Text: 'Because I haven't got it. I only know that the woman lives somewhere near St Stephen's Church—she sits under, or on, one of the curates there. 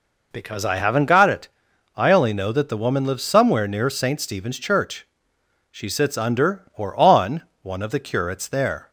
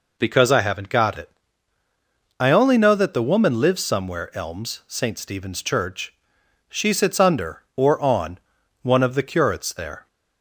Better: first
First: none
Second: says "elms" for "near"; at 4.3 s

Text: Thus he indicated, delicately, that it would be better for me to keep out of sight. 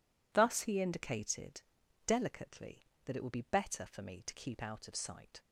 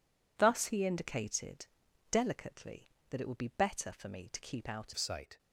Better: first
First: none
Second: changes voice at "of"; from 4.9 s on; 0.4 s long

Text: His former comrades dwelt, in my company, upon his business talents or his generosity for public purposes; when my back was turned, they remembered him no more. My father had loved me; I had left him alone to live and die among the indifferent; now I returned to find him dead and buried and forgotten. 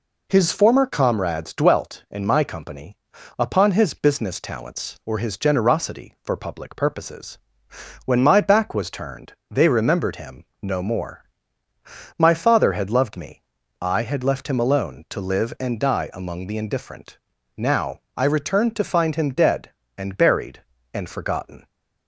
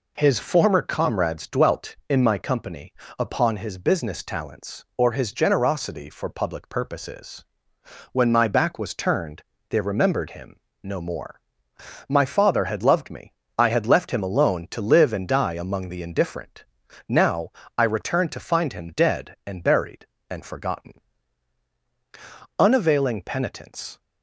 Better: first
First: pauses between "him" and "no"; slight; at 10.4 s; 0.16 s long // pauses between "now" and "I"; slight; at 17.9 s; 0.16 s long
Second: pauses between "him" and "no"; slight; at 10.5 s; 0.24 s long // pauses between "now" and "I"; slight; at 17.5 s; 0.26 s long // goes on to say "Unavailing penitence"; from 22.5 s on; 1.4 s long

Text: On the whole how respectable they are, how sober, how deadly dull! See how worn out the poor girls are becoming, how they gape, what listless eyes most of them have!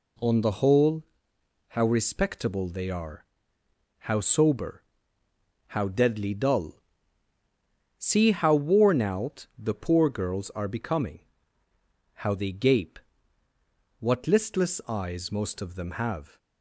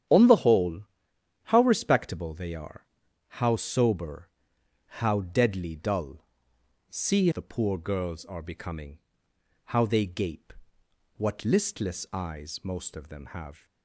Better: first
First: pauses between "whole" and "how"; noticeable; at 1.0 s; 0.66 s long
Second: starts louder than the rest; strong; until 1.7 s; 9.5 dB // pauses between "whole" and "how"; noticeable; at 0.8 s; 0.62 s long // skips "how worn out"; at 7.3 s

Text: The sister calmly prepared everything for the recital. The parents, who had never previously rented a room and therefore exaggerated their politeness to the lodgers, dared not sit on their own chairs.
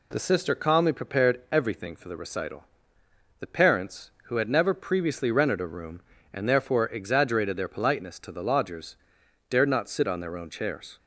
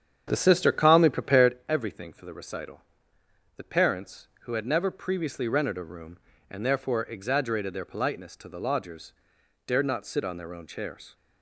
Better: first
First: none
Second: starts louder than the rest; strong; until 1.6 s; 8.5 dB

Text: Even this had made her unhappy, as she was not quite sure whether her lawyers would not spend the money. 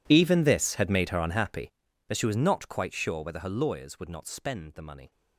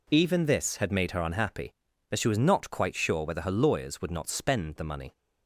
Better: second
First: gets quieter; strong; throughout; 22 dB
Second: none

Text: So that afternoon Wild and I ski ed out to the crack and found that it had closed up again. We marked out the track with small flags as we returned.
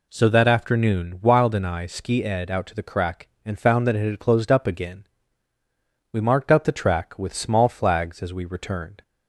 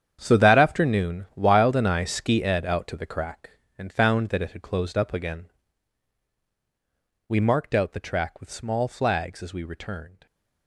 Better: first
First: none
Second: gets quieter; strong; throughout; 13 dB

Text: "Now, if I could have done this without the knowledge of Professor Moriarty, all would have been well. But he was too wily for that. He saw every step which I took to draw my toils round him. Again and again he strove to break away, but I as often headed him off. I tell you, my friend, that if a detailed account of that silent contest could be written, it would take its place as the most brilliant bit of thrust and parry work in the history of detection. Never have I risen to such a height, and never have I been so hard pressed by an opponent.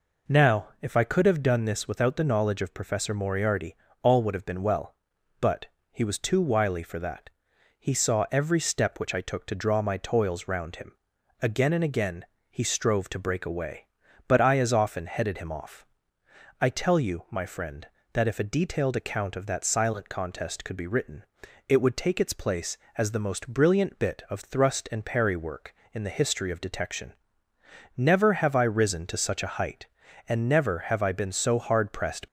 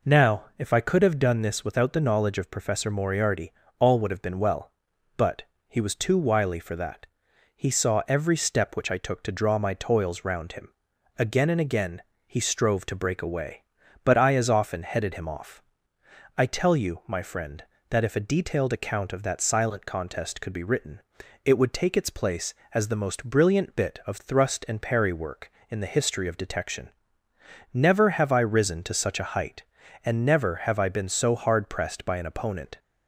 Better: second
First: pauses between "But" and "he"; slight; at 5.6 s; 0.26 s long // pauses between "again" and "he"; slight; at 12.2 s; 0.24 s long // stops before "by an opponent"; at 32.2 s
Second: pauses between "But" and "he"; slight; at 5.4 s; 0.26 s long // pauses between "again" and "he"; slight; at 12.0 s; 0.24 s long

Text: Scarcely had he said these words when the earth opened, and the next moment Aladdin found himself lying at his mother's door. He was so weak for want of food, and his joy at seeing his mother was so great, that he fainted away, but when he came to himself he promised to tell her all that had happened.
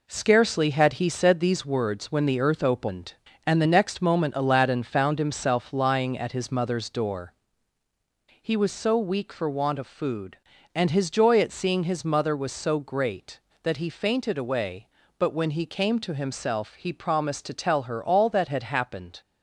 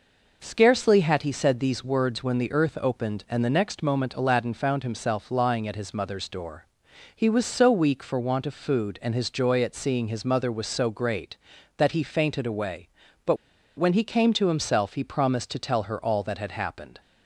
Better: first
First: none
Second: pauses between "but" and "when"; at 13.3 s; 0.41 s long

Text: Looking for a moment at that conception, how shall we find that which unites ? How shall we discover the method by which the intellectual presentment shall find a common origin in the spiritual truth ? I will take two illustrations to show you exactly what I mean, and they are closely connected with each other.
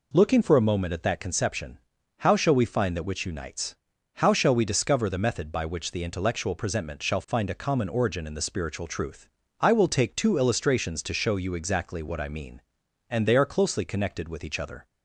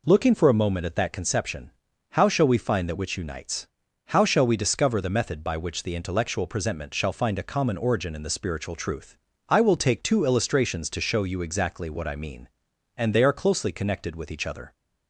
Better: neither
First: none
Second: none

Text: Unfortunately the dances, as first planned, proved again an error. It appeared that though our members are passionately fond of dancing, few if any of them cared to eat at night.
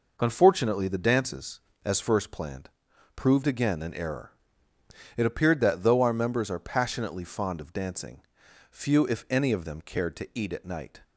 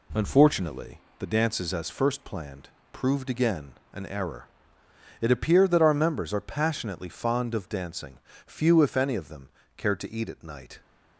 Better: first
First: none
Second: pauses between "Unfortunately" and "the"; slight; at 0.9 s; 0.20 s long // pauses between "again" and "an"; slight; at 3.7 s; 0.20 s long // skips "though"; at 5.8 s // pauses between "them" and "cared"; slight; at 9.4 s; 0.28 s long

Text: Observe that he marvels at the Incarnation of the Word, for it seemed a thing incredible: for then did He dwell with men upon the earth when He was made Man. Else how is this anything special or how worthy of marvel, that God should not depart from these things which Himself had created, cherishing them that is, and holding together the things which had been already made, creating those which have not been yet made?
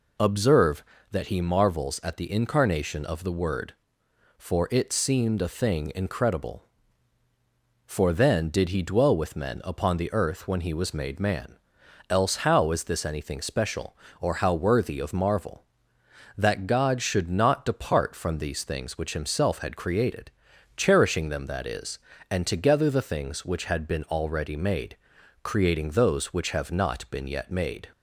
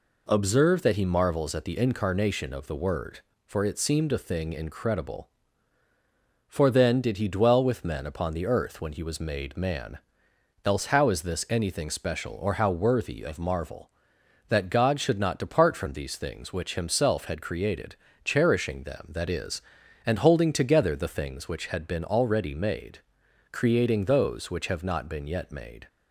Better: second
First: skips "holding"; at 22.4 s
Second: none

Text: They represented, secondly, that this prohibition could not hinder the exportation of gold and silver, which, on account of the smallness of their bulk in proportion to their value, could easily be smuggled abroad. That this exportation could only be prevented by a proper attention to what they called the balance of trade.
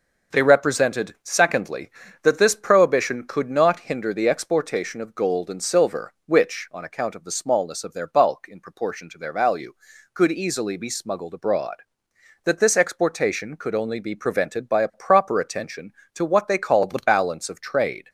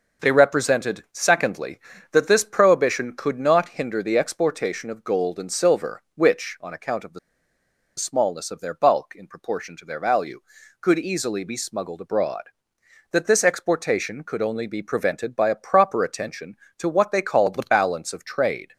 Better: first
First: none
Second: pauses between "the" and "smallness"; noticeable; at 7.1 s; 0.79 s long

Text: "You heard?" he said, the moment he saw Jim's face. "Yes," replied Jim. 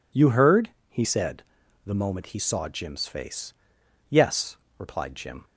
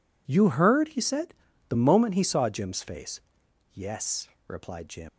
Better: first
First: none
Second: leaves "Jim" unfinished; at 5.0 s; 125 ms

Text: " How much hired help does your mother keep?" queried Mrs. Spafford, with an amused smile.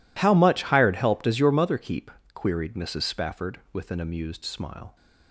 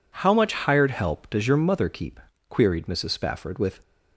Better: first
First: none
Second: stops before "an amused smile"; at 3.8 s

